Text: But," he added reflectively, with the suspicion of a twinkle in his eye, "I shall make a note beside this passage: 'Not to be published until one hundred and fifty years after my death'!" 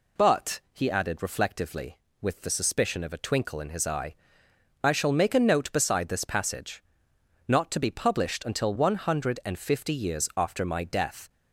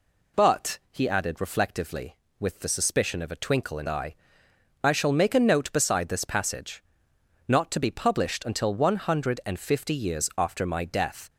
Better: first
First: none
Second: skips "his"; at 3.8 s

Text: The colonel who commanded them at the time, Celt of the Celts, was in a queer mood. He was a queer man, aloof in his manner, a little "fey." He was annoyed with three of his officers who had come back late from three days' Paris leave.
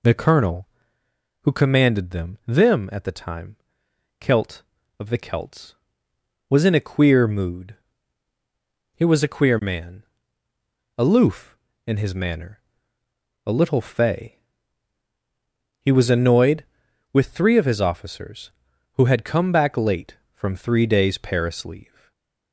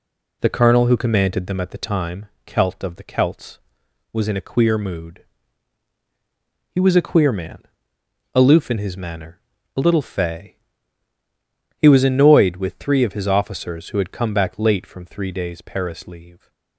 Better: second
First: says "them" twice; at 2.4 s // stays silent after the last word; slight; from 21.8 s on; 0.7 s long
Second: none

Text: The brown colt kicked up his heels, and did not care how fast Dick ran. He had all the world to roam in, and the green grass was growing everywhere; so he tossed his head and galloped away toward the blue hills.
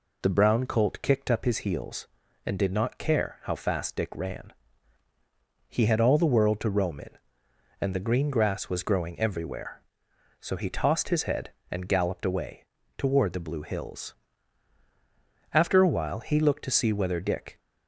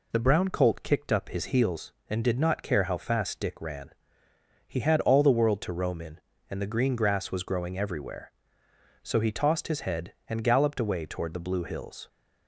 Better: second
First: pauses between "away" and "toward"; slight; at 12.6 s; 0.32 s long // goes on to say "After a while he looked to see whether Dick"; strong; from 15.5 s on; 2.0 s long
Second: none

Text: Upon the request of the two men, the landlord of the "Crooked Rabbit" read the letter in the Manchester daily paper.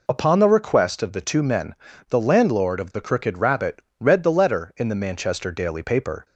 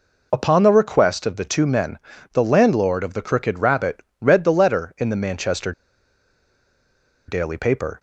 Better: first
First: pauses between "Rabbit" and "read"; slight; at 3.7 s; 0.20 s long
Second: pauses between "Rabbit" and "read"; slight; at 3.9 s; 0.20 s long // pauses between "Manchester" and "daily"; strong; at 5.7 s; 1.5 s long

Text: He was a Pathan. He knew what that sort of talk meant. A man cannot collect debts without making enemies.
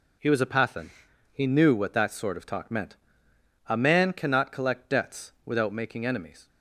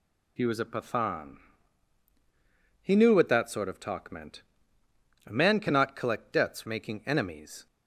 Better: first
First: none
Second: skips "without"; at 6.6 s

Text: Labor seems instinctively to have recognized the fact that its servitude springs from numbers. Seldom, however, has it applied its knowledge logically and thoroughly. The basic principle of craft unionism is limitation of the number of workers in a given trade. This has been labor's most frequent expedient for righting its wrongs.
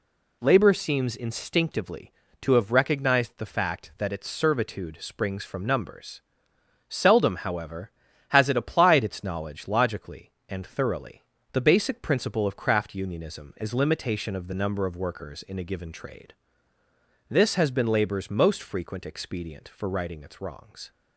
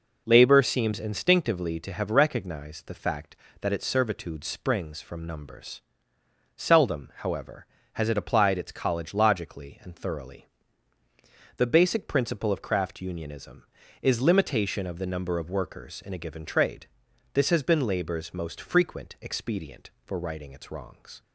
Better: first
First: none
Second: says "college" for "knowledge"; at 8.7 s

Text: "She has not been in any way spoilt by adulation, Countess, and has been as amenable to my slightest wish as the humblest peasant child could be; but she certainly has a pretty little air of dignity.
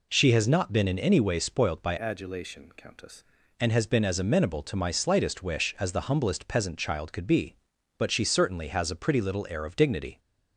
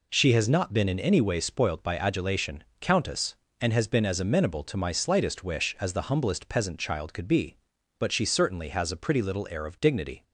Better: second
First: changes voice from "adulation" to "Countess"; from 1.9 to 3.2 s; 1.3 s long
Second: none

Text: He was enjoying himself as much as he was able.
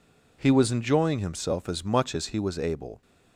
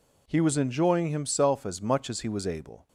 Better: neither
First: none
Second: none

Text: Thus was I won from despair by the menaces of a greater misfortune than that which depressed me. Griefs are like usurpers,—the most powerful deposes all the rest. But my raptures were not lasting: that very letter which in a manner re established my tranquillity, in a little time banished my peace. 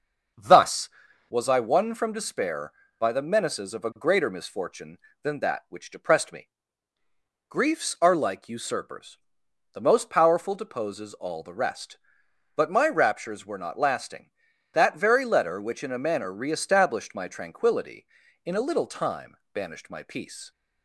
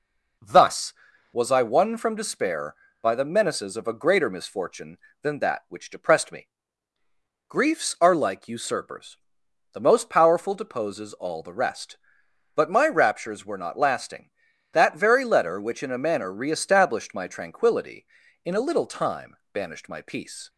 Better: second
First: starts louder than the rest; until 1.3 s; 6.5 dB // pauses between "time" and "banished"; slight; at 19.3 s; 0.18 s long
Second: pauses between "time" and "banished"; slight; at 19.3 s; 0.18 s long

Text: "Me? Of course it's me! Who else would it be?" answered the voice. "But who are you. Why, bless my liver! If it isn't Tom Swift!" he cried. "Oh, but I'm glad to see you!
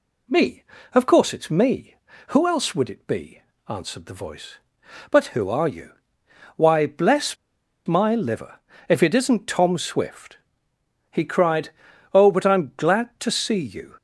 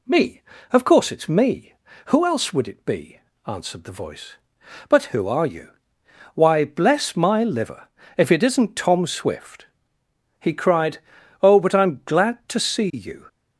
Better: second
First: pauses between "bless" and "my"; noticeable; at 7.3 s; 0.50 s long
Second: none

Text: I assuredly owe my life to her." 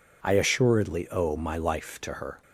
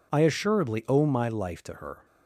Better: neither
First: none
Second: none

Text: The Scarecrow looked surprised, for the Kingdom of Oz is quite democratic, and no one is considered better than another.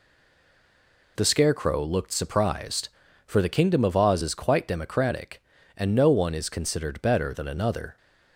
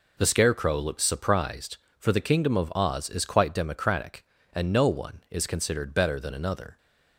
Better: second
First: stays silent before the first word; until 1.1 s; 1.1 s long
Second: none

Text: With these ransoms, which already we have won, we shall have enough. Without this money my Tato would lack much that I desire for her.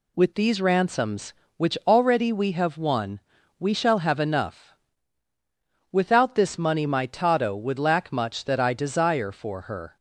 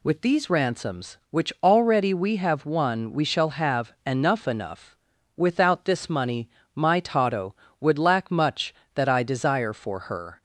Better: first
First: none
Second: says "enough" twice; at 4.4 s // pauses between "money" and "my"; slight; at 6.4 s; 0.24 s long

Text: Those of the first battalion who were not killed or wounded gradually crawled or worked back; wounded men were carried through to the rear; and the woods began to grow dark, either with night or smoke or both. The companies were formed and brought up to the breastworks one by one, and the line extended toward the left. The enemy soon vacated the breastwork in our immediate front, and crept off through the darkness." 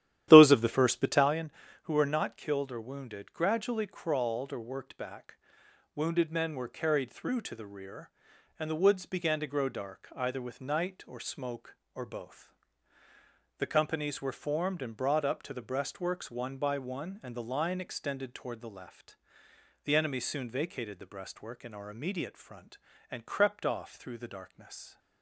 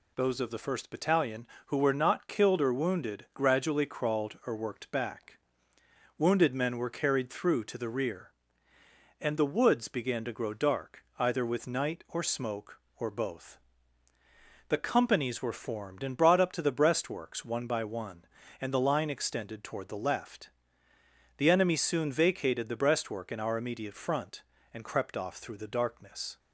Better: second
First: starts louder than the rest; strong; until 1.4 s; 12 dB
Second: none

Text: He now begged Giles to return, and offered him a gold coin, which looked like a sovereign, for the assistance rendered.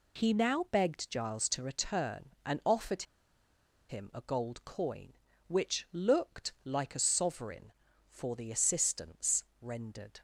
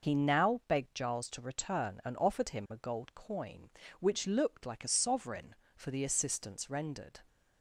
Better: second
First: pauses between "offered" and "him"; noticeable; at 3.0 s; 0.86 s long // pauses between "assistance" and "rendered"; slight; at 9.4 s; 0.20 s long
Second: none

